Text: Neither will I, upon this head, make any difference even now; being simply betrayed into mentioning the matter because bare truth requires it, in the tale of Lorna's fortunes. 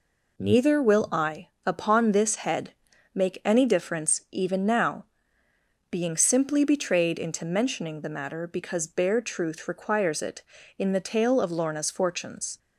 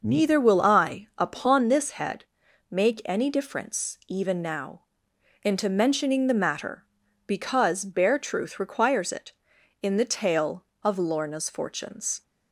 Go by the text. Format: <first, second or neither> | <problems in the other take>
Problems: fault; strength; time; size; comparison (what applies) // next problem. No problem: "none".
first | skips "being simply betrayed"; at 5.1 s